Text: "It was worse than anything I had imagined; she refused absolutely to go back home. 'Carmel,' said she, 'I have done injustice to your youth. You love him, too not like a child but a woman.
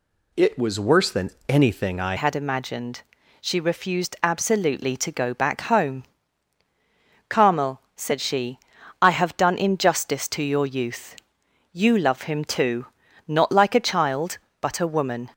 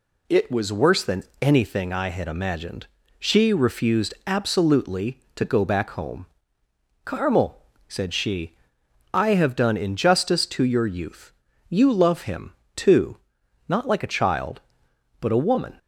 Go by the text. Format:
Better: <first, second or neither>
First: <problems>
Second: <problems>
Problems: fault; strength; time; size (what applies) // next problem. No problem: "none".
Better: second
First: pauses between "than" and "anything"; slight; at 1.2 s; 0.18 s long // changes voice at "had"; from 2.1 s on; 13.1 s long // pauses between "too" and "not"; at 12.8 s; 0.40 s long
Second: pauses between "than" and "anything"; slight; at 1.2 s; 0.18 s long // pauses between "too" and "not"; noticeable; at 13.1 s; 0.50 s long